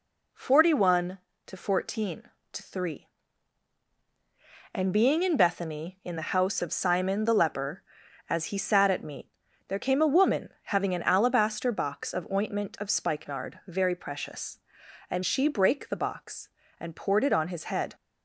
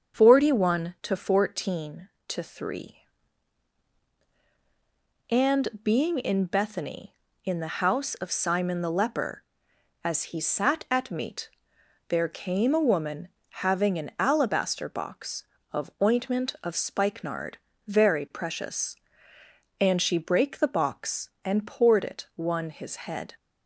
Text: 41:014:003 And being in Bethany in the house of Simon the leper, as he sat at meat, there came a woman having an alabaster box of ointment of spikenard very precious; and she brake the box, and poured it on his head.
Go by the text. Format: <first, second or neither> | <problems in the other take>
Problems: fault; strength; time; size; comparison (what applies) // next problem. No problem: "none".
first | starts louder than the rest; until 1.2 s; 6.5 dB // pauses between "And" and "being"; slight; at 5.6 s; 0.16 s long // pauses between "woman" and "having"; at 13.2 s; 0.38 s long // pauses between "spikenard" and "very"; slight; at 17.5 s; 0.28 s long // says "one" for "on"; at 22.3 s